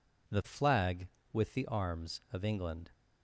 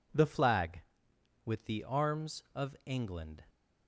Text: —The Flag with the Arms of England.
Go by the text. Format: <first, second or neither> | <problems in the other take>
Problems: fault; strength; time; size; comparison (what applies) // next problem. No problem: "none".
neither | none